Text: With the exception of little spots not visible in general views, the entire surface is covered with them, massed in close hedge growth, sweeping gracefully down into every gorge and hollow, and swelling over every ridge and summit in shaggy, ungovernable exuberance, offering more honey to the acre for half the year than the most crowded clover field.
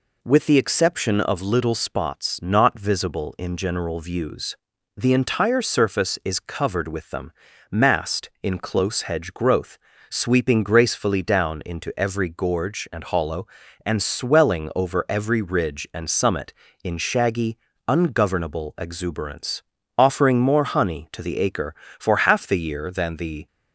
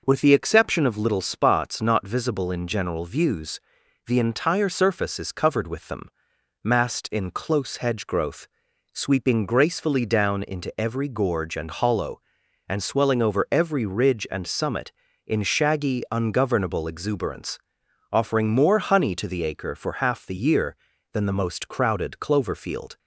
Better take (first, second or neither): second